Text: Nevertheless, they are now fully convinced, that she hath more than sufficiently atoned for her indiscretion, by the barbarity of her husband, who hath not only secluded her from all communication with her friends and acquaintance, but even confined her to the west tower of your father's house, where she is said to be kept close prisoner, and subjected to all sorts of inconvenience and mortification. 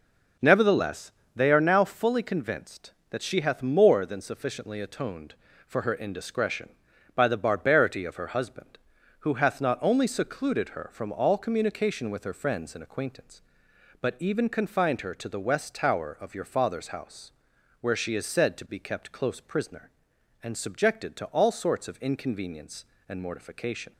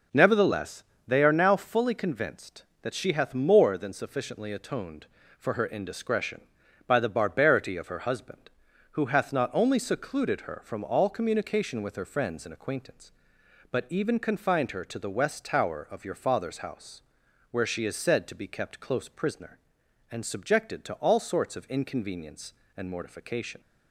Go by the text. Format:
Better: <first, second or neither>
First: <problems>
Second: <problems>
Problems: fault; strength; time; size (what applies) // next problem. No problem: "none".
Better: neither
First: none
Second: none